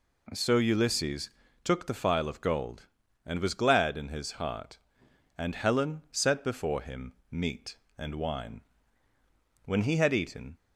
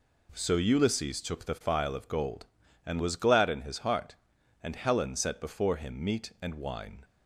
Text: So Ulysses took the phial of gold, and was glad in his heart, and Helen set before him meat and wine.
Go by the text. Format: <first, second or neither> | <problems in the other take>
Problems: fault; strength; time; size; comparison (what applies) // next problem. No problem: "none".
second | pauses between "Ulysses" and "took"; slight; at 1.2 s; 0.34 s long // pauses between "him" and "meat"; slight; at 7.1 s; 0.18 s long // goes on to say "When he had eaten"; noticeable; from 9.6 s on; 0.90 s long